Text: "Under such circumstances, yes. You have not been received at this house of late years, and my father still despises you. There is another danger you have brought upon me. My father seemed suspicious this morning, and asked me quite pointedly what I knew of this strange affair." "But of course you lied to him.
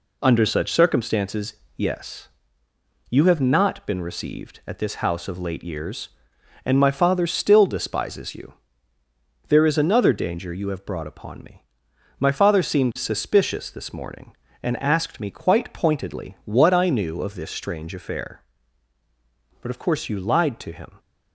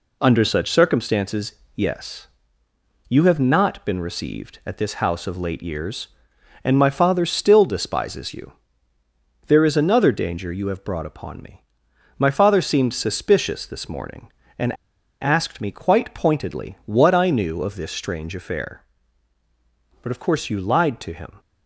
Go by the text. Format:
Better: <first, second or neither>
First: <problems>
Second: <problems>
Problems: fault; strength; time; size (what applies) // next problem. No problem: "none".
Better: first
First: none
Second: pauses between "and" and "asked"; noticeable; at 14.7 s; 0.48 s long